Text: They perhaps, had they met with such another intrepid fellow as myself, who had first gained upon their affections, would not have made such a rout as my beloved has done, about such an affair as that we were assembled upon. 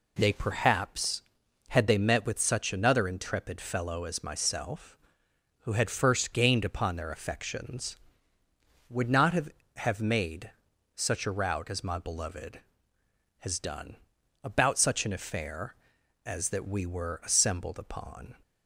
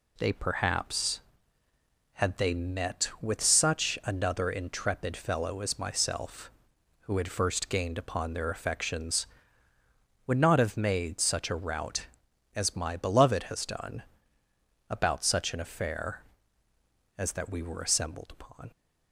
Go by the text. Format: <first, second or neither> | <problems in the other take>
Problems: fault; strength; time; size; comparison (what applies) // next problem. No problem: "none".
second | says "have" twice; at 9.7 s // pauses between "made" and "such"; noticeable; at 10.4 s; 0.46 s long